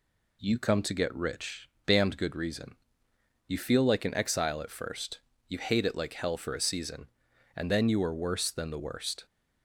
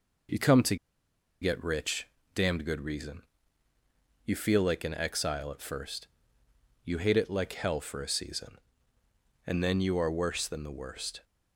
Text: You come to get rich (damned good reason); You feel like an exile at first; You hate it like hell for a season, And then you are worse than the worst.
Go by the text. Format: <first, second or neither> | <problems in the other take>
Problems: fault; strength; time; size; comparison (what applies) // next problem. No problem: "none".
first | pauses between "to" and "get"; noticeable; at 0.7 s; 0.65 s long